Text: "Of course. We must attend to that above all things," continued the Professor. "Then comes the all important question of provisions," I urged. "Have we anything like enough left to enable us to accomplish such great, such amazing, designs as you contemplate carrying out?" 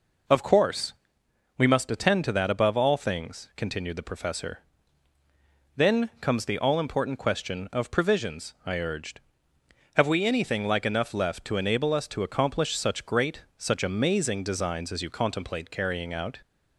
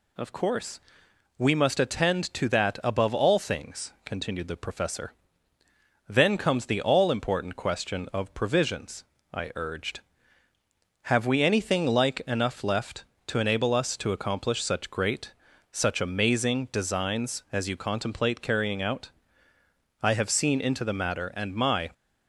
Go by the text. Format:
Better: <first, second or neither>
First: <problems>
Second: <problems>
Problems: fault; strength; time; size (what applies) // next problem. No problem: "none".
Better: first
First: none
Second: goes on to say "I have seen into the matter and my"; strong; from 20.0 s on; 1.8 s long